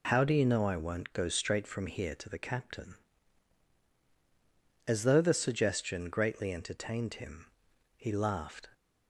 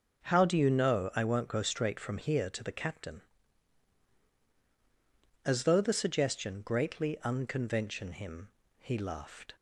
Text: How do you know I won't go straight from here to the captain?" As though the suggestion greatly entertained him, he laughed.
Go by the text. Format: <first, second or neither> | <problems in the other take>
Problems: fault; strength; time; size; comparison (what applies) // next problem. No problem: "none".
first | starts louder than the rest; until 1.3 s; 6 dB // says "unconvention" for "entertained"; at 7.2 s